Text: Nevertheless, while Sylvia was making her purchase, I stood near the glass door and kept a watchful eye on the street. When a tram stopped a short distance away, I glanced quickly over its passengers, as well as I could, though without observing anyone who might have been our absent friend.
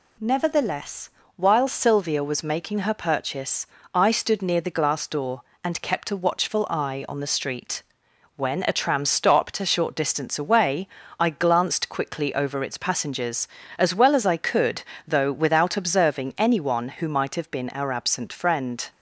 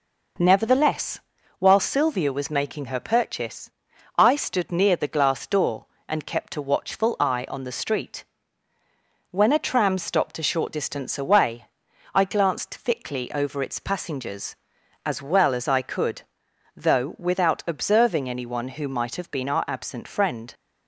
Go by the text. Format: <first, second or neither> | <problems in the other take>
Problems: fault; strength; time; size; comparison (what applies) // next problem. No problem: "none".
first | says "thickly" for "quickly"; at 12.7 s